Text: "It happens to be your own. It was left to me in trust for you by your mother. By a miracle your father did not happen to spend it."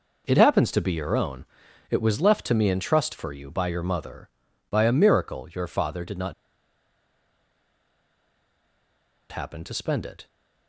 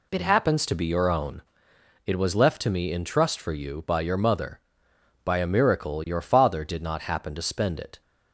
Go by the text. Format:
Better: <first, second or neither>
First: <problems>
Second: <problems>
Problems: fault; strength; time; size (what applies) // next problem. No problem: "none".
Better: second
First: pauses between "not" and "happen"; strong; at 6.3 s; 2.9 s long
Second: none